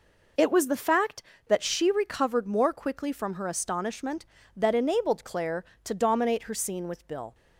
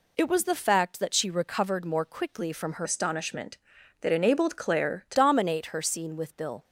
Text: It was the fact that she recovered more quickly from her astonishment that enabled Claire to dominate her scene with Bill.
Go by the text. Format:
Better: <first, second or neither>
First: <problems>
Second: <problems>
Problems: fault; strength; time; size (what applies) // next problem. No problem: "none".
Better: first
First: none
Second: changes voice from "astonishment" to "to"; from 2.8 to 5.1 s; 2.3 s long